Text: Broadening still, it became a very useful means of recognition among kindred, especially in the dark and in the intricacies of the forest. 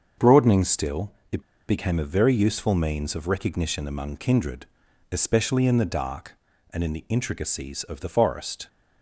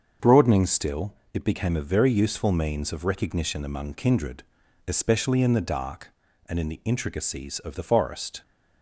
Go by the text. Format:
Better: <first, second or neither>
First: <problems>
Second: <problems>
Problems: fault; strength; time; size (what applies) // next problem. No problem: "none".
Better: second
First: starts louder than the rest; until 1.3 s; 7 dB // pauses between "it" and "became"; slight; at 1.4 s; 0.26 s long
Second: starts louder than the rest; until 1.3 s; 6.5 dB